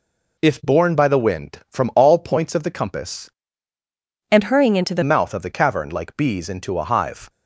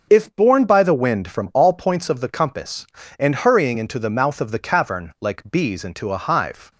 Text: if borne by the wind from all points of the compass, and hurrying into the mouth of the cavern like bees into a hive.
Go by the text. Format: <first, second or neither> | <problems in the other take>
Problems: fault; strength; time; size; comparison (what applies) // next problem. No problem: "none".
second | changes voice from "and" to "the"; from 4.3 to 5.0 s; 0.7 s long